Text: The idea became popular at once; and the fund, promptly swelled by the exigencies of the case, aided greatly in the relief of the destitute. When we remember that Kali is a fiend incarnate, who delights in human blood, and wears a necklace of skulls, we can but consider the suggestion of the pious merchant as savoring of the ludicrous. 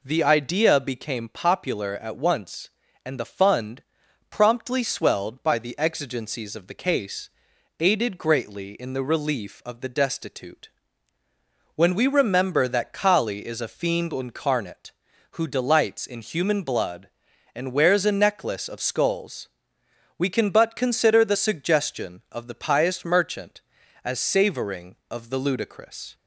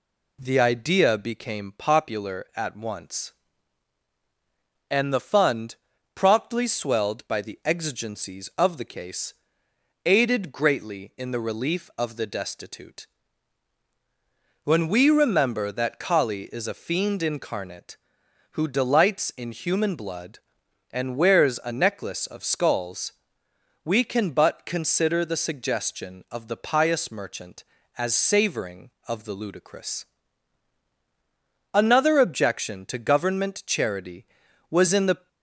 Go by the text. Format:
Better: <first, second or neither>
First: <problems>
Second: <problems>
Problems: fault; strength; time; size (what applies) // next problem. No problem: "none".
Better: first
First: none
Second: goes on to say "Another objection to government charity was in the"; strong; from 31.7 s on; 3.5 s long